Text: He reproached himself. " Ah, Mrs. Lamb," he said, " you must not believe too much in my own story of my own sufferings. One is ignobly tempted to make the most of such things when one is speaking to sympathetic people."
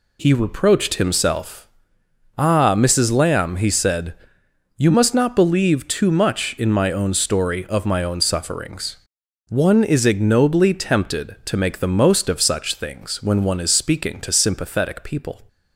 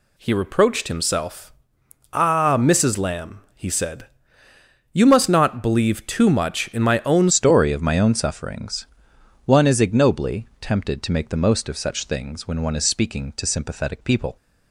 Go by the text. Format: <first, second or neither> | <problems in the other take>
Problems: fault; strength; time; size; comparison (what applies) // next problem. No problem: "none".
first | changes voice at "story"; from 7.3 s on; 7.0 s long